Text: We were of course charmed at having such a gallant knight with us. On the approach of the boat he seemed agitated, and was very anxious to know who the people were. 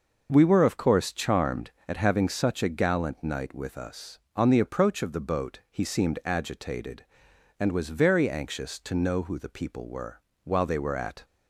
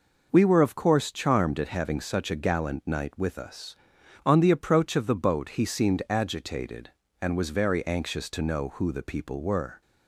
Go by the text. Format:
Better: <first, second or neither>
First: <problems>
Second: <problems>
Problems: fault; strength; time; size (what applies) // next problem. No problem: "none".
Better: second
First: goes on to say "While they were at"; noticeable; from 10.4 s on; 0.80 s long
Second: none